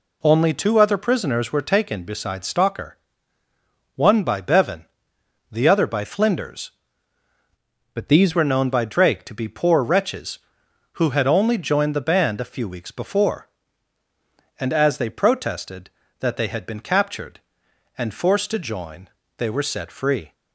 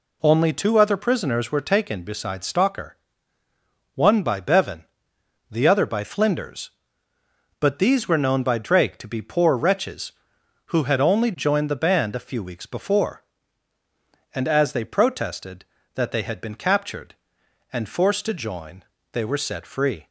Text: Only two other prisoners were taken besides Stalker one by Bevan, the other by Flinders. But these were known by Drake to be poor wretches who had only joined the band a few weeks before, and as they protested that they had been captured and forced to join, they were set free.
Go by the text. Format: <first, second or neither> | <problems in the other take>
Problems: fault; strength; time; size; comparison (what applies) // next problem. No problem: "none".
second | pauses between "Stalker" and "one"; at 2.9 s; 1.0 s long; also in the second // changes voice from "But" to "these"; from 7.9 to 8.3 s; 0.4 s long